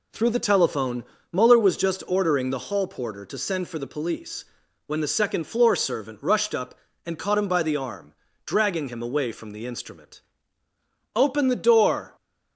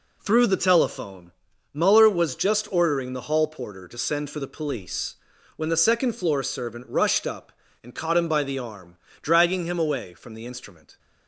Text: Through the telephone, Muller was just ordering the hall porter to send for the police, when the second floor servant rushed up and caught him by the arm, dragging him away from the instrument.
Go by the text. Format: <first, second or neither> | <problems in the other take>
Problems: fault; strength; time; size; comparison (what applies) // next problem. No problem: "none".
second | goes on to say "Open the door"; noticeable; from 11.1 s on; 1.0 s long